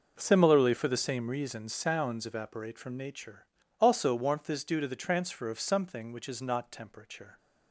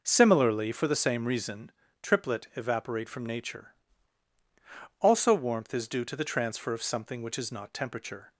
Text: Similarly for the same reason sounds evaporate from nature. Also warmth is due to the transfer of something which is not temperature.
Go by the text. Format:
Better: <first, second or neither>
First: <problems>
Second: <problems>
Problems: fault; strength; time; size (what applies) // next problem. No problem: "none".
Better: first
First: none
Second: says "triplet" for "sounds"; at 2.0 s